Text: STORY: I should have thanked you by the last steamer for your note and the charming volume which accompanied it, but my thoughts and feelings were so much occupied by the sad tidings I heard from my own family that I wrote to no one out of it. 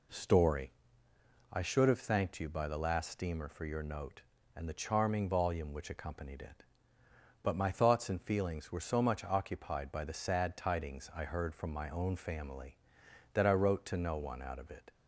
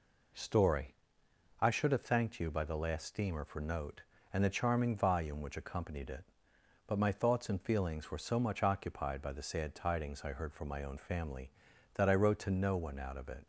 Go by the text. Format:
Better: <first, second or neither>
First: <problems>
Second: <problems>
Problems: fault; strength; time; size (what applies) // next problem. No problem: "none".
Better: first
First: none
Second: skips "your"; at 3.5 s